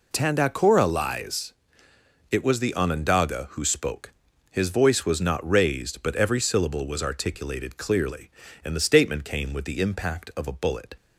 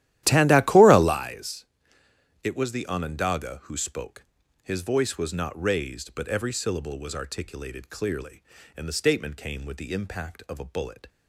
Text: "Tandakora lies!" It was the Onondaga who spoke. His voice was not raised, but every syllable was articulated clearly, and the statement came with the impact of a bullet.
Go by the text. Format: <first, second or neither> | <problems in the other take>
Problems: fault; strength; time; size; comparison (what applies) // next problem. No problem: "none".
first | starts louder than the rest; strong; until 1.2 s; 13.5 dB